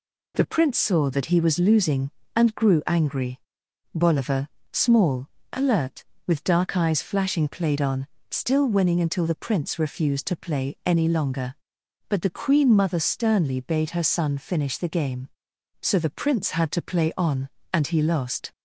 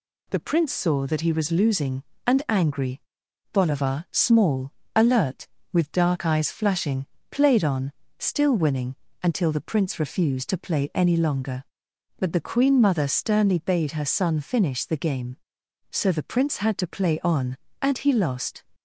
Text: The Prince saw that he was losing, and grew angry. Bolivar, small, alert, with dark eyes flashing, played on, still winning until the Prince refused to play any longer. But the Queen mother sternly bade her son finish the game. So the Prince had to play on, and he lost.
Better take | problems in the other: first | skips "grew"; at 2.4 s // pauses between "winning" and "until"; slight; at 8.9 s; 0.28 s long

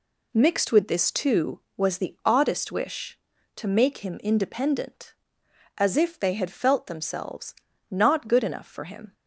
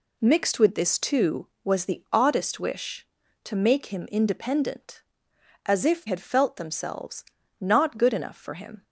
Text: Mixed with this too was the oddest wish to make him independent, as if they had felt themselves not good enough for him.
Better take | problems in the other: first | skips "they"; at 6.0 s // pauses between "themselves" and "not"; slight; at 7.2 s; 0.34 s long; slight in the first

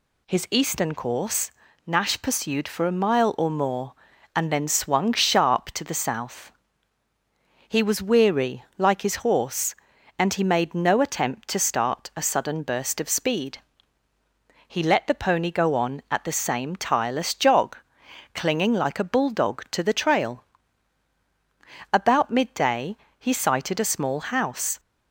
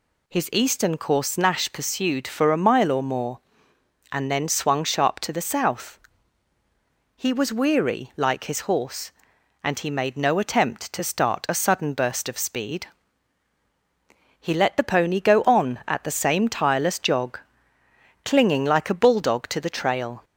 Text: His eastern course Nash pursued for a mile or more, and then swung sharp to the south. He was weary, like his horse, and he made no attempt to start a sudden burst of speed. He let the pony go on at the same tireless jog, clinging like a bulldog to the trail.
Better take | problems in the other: second | pauses between "course" and "Nash"; slight; at 1.5 s; 0.34 s long // goes on to say "About midday he sighted a small house"; strong; from 21.9 s on; 2.8 s long

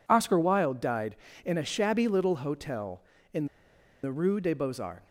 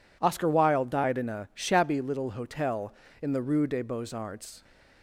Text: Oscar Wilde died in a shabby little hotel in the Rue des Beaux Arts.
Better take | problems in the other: second | pauses between "in" and "the"; noticeable; at 3.4 s; 0.57 s long

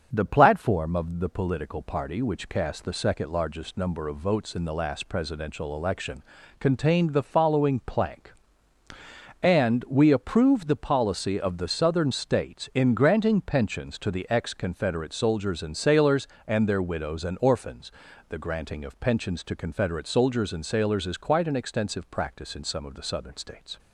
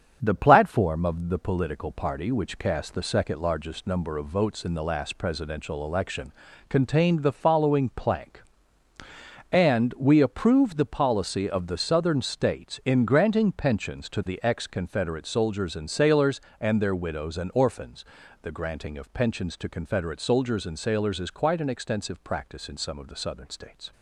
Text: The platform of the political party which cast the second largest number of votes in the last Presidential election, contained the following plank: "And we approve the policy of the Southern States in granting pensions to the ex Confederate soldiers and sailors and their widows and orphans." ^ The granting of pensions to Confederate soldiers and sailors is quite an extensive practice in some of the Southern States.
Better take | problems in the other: first | gets quieter; noticeable; throughout; 5 dB // starts louder than the rest; strong; until 1.2 s; 7.5 dB; also in the first

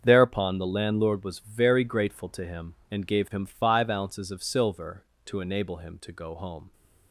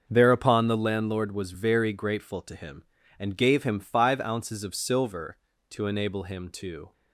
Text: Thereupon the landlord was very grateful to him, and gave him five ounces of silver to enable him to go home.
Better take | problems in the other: first | starts louder than the rest; until 1.0 s; 6 dB; strong in the first // stops before "go home"; at 6.9 s

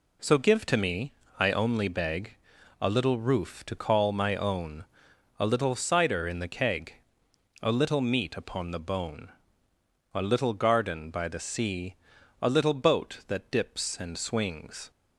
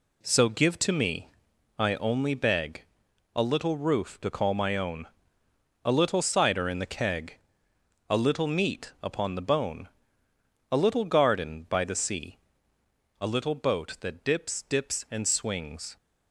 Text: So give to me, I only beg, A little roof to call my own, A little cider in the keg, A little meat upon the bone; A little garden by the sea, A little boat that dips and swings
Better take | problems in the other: first | says "dips" twice; at 14.6 s

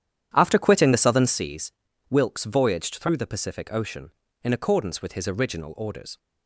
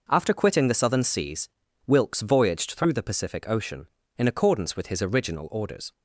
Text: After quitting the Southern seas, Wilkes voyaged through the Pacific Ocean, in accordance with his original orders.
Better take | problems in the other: second | starts louder than the rest; strong; until 1.4 s; 10 dB

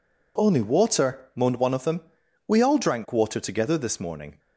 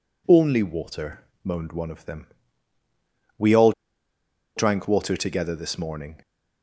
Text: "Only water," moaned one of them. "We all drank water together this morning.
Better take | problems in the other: first | pauses between "all" and "drank"; noticeable; at 3.7 s; 0.84 s long

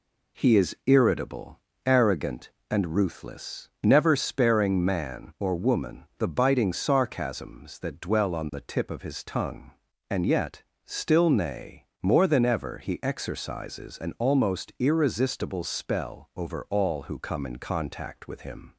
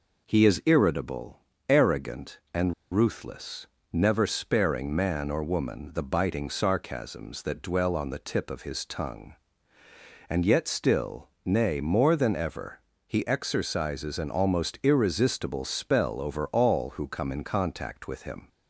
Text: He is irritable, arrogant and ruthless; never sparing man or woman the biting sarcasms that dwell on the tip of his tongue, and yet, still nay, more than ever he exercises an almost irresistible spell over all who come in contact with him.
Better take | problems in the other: first | pauses between "and" and "ruthless"; slight; at 2.7 s; 0.20 s long // pauses between "still" and "nay"; slight; at 11.2 s; 0.16 s long // pauses between "ever" and "he"; slight; at 12.7 s; 0.26 s long

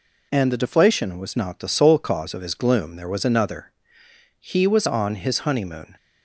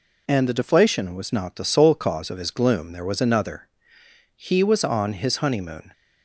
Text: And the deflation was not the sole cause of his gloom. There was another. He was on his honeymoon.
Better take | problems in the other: neither | none

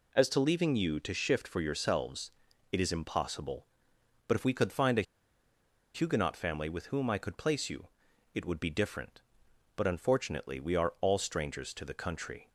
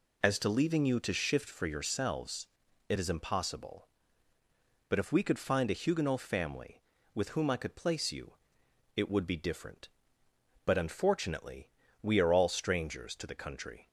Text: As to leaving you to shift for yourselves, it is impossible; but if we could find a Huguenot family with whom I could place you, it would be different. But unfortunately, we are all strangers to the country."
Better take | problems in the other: second | pauses between "a" and "Huguenot"; noticeable; at 5.0 s; 0.92 s long

